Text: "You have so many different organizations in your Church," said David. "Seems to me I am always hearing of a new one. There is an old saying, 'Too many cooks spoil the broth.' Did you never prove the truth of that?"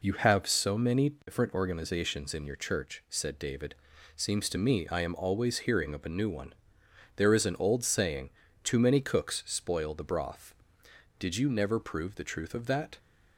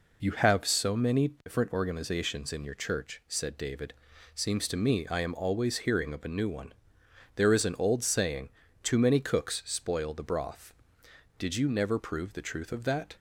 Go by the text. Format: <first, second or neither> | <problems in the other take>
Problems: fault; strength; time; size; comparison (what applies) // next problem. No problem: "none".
neither | none